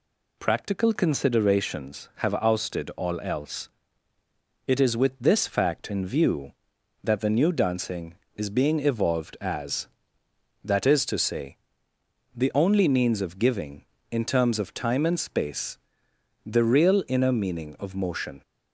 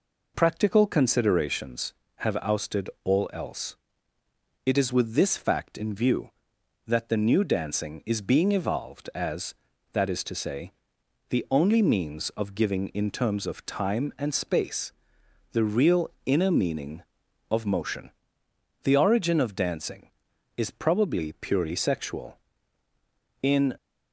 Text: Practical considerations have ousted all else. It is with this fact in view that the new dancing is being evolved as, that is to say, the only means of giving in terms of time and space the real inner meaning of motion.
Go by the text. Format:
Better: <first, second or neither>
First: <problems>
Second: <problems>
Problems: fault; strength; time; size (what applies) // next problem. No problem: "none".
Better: first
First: pauses between "space" and "the"; noticeable; at 15.7 s; 0.68 s long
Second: pauses between "ousted" and "all"; slight; at 2.8 s; 0.16 s long // pauses between "space" and "the"; noticeable; at 14.9 s; 0.62 s long // pauses between "real" and "inner"; slight; at 16.0 s; 0.16 s long // goes on to say "The origin of dancing is probably purely sexual In"; strong; from 18.8 s on; 4.9 s long